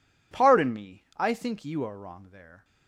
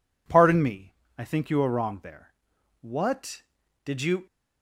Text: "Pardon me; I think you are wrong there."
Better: first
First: none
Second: goes on to say "What did you"; from 2.7 s on; 1.4 s long

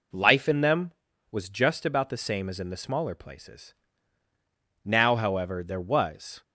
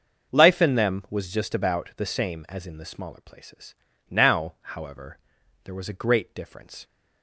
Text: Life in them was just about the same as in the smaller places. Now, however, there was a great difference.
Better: second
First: stops before "a great difference"; at 6.4 s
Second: none

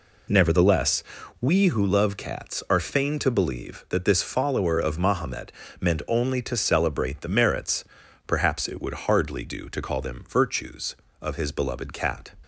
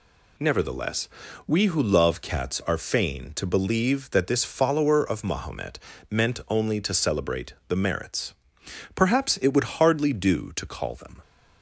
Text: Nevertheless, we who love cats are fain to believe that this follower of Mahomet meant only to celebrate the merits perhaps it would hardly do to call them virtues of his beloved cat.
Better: first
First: pauses between "Mahomet" and "meant"; slight; at 5.5 s; 0.30 s long // pauses between "merits" and "perhaps"; at 7.8 s; 0.44 s long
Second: pauses between "Mahomet" and "meant"; slight; at 5.7 s; 0.32 s long // pauses between "celebrate" and "the"; slight; at 7.5 s; 0.16 s long // pauses between "merits" and "perhaps"; noticeable; at 8.3 s; 0.60 s long // stops before "virtues of his beloved cat"; at 11.2 s

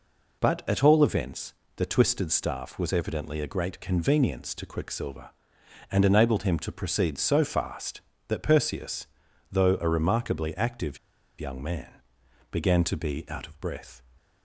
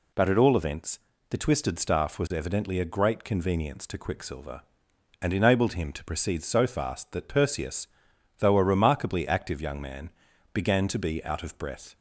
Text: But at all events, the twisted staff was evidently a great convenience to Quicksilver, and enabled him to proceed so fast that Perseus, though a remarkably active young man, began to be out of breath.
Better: second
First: pauses between "active" and "young"; at 10.9 s; 0.41 s long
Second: none

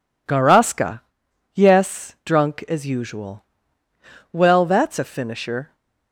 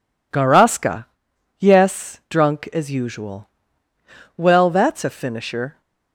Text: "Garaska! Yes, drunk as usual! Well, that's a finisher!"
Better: neither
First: none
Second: none

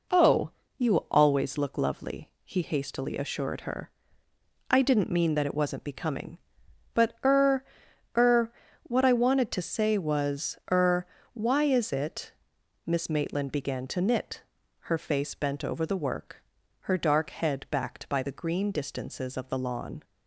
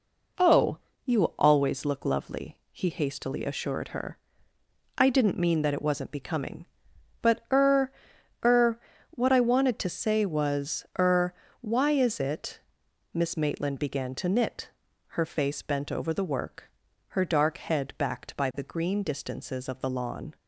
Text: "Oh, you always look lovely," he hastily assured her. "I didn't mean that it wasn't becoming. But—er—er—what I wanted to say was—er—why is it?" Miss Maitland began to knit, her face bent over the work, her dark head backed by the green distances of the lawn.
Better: neither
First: none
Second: none

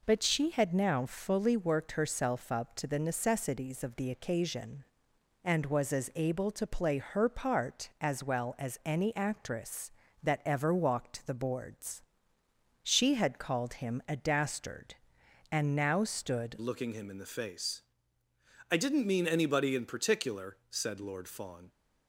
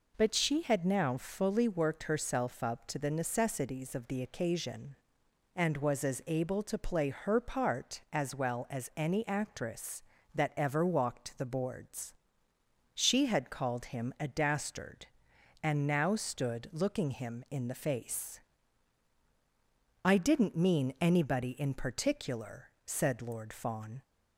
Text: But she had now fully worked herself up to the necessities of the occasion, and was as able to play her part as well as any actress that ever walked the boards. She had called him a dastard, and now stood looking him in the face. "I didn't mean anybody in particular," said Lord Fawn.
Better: second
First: changes voice at "looking"; from 16.5 s on; 5.1 s long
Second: none

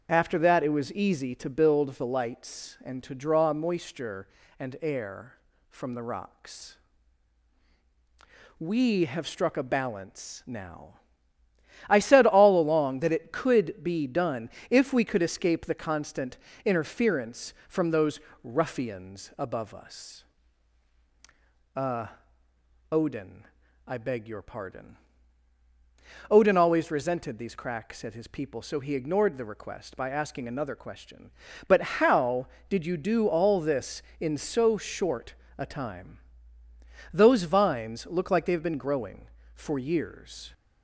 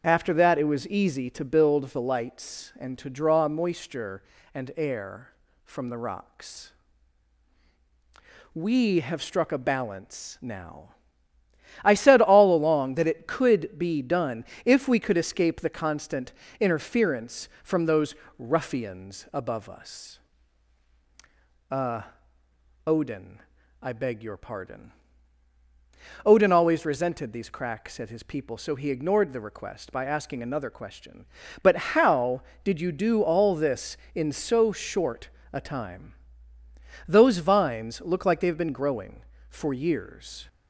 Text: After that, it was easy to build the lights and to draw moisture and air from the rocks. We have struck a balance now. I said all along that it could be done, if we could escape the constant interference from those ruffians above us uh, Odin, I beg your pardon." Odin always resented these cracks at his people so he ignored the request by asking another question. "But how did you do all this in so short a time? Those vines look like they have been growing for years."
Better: neither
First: starts louder than the rest; until 1.1 s; 7 dB // pauses between "constant" and "interference"; slight; at 16.3 s; 0.26 s long // pauses between "those" and "ruffians"; slight; at 18.1 s; 0.24 s long // pauses between "us" and "uh"; strong; at 20.2 s; 1.5 s long // pauses between "But" and "how"; slight; at 31.8 s; 0.20 s long // pauses between "short" and "a"; slight; at 35.3 s; 0.24 s long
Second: starts louder than the rest; until 1.0 s; 7 dB // pauses between "constant" and "interference"; slight; at 16.3 s; 0.26 s long // pauses between "those" and "ruffians"; slight; at 18.1 s; 0.24 s long // pauses between "us" and "uh"; strong; at 20.1 s; 1.5 s long // pauses between "But" and "how"; slight; at 31.7 s; 0.20 s long // pauses between "short" and "a"; slight; at 35.2 s; 0.24 s long

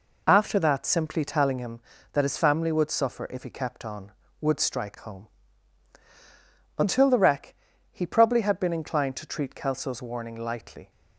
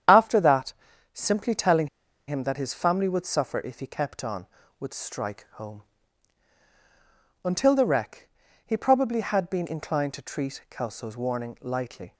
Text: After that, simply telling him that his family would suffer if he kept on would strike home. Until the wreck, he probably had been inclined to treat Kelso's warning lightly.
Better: first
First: none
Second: starts louder than the rest; strong; until 1.4 s; 8.5 dB // pauses between "telling" and "him"; at 1.8 s; 0.39 s long

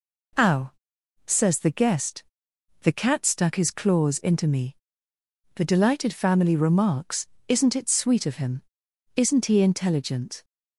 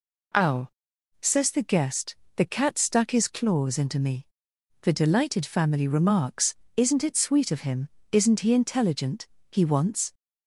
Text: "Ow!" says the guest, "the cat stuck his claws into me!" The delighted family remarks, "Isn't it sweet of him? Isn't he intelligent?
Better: first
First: none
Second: goes on to say "He wants"; noticeable; from 9.4 s on; 0.64 s long

